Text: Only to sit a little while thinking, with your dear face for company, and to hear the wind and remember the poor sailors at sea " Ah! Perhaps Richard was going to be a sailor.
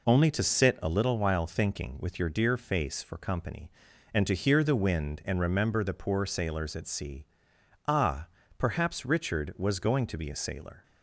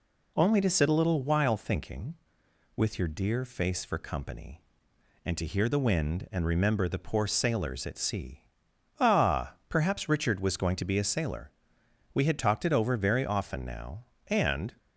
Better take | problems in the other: first | goes on to say "We had talked it over very often now and"; strong; from 12.1 s on; 2.6 s long

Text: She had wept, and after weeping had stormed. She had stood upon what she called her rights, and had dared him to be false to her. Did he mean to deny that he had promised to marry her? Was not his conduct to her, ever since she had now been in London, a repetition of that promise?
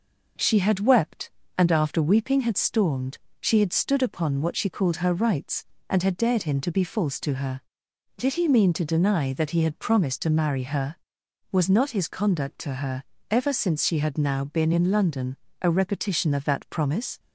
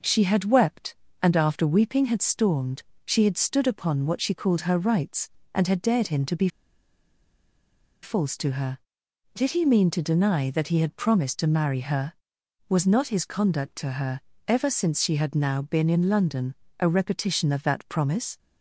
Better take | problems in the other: first | pauses between "be" and "false"; strong; at 6.4 s; 1.5 s long

